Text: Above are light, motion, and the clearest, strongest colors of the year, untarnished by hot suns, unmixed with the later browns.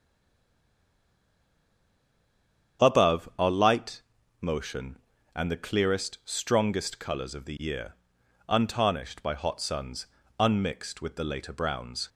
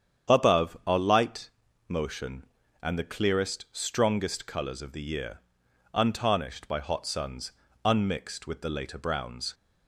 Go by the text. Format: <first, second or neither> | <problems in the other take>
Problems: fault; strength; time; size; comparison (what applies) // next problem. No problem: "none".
second | stays silent before the first word; strong; until 2.7 s; 2.7 s long // starts louder than the rest; strong; until 3.9 s; 8.5 dB; strong in the second